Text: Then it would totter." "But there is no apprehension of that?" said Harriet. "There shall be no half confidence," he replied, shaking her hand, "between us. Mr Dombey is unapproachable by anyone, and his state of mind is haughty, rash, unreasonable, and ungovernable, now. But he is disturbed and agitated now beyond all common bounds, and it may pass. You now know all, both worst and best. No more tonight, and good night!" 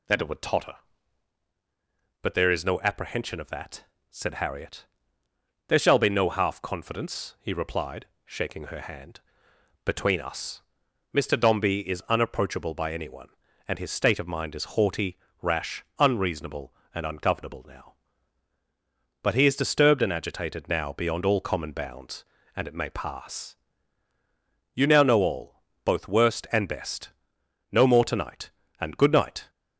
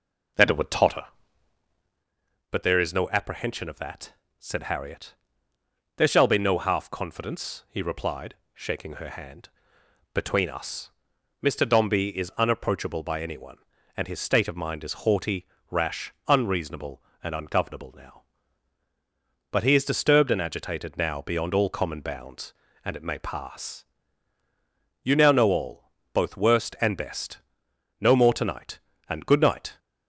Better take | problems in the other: first | starts louder than the rest; noticeable; until 2.2 s; 5 dB

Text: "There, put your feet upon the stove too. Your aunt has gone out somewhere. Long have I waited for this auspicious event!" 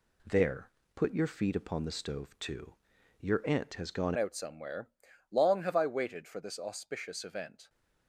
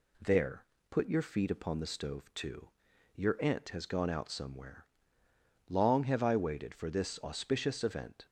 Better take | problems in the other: second | changes voice at "out"; from 4.1 s on; 3.5 s long

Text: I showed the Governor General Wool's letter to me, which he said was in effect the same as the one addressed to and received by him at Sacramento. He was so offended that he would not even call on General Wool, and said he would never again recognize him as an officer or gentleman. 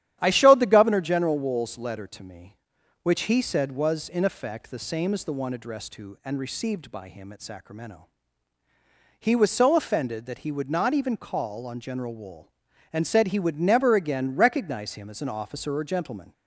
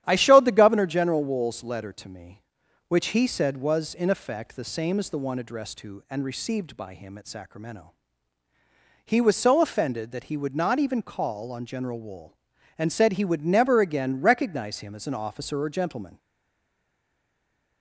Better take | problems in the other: first | starts louder than the rest; strong; until 1.0 s; 11 dB; strong in the first // stays silent after the last word; noticeable; from 16.1 s on; 1.7 s long

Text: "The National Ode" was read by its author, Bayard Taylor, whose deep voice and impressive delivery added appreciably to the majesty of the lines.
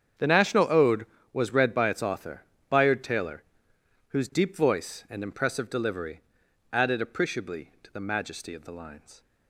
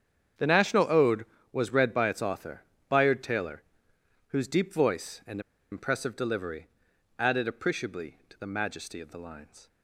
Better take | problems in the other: first | starts louder than the rest; strong; until 1.6 s; 8 dB; strong in the first // pauses between "and" and "impressive"; slight; at 5.4 s; 0.31 s long // pauses between "delivery" and "added"; noticeable; at 6.6 s; 0.52 s long; noticeable in the first

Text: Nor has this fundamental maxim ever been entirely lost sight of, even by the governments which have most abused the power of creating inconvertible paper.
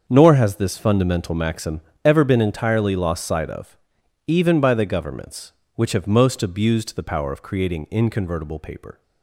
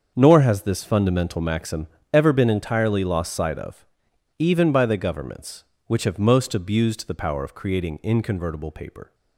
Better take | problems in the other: neither | starts louder than the rest; the same in both // pauses between "maxim" and "ever"; slight; the same in both

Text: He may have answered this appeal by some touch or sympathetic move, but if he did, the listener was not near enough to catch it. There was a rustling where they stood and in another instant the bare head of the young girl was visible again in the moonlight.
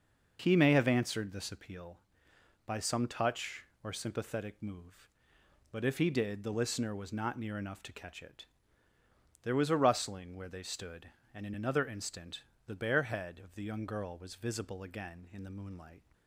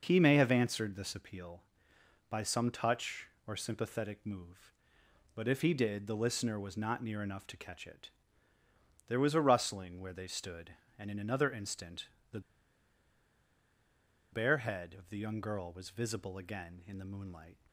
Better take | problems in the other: first | pauses between "instant" and "the"; slight; at 12.0 s; 0.24 s long; slight in the first // pauses between "the" and "bare"; strong; at 12.3 s; 1.9 s long

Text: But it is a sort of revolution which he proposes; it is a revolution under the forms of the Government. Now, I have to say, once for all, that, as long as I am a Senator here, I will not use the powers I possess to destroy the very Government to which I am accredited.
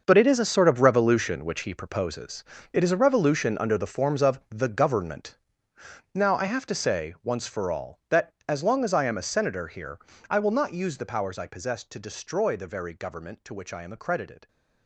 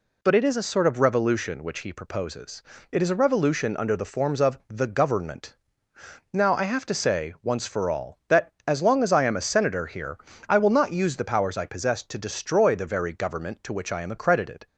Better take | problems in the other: second | gets quieter; strong; throughout; 13.5 dB

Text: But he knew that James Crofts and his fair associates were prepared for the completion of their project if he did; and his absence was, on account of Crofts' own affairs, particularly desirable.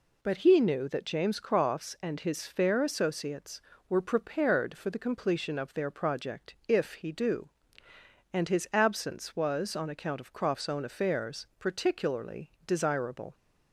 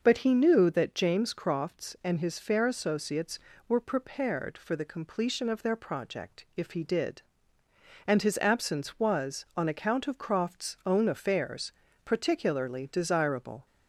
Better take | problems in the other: second | says "do" for "did"; at 7.1 s

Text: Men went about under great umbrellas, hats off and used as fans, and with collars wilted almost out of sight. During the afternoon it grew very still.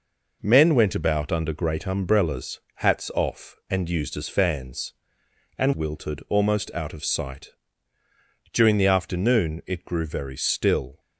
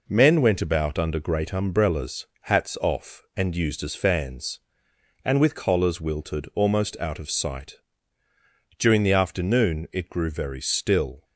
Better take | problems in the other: second | skips "with collars"; at 5.7 s

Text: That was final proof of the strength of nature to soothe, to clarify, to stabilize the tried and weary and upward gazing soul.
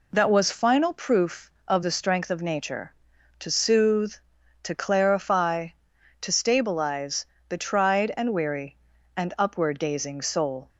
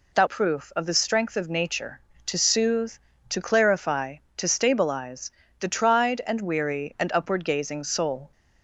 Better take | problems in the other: first | skips "was final"; at 0.2 s // pauses between "stabilize" and "the"; slight; at 5.3 s; 0.28 s long; slight in the first

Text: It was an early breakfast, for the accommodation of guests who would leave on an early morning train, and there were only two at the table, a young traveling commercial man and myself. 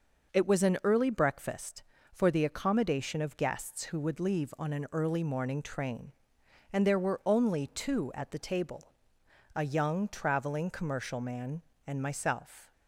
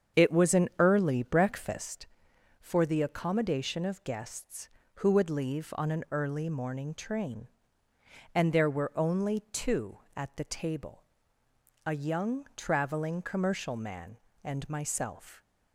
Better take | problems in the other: first | starts louder than the rest; strong; until 2.0 s; 7.5 dB

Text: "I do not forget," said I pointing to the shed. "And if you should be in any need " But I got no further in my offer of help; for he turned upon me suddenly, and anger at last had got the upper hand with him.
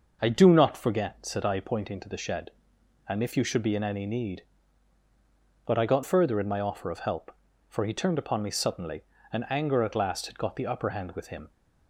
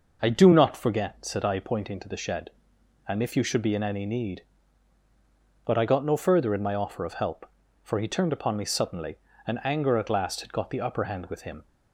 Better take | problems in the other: second | starts louder than the rest; noticeable; until 1.2 s; 6 dB // skips "no"; at 6.0 s

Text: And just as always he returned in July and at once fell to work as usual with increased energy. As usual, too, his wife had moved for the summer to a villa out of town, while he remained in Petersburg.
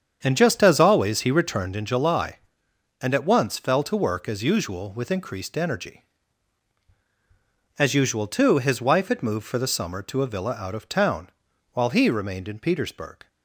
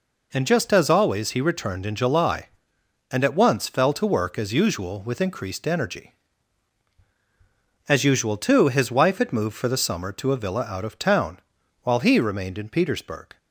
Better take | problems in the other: second | starts louder than the rest; strong; until 1.8 s; 7.5 dB

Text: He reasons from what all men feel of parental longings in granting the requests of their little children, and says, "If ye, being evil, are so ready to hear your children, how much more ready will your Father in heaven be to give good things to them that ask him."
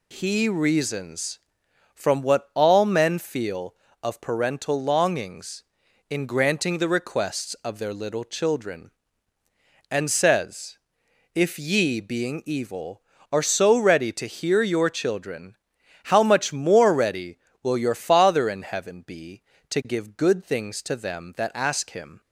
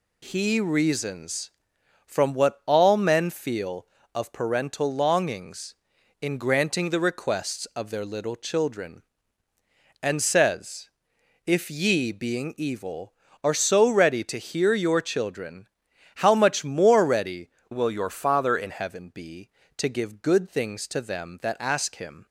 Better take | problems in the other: first | changes voice from "will" to "in"; from 17.7 to 18.7 s; 1.0 s long

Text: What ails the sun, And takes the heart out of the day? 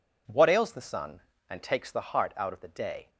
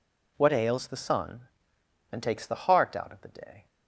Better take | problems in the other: neither | none

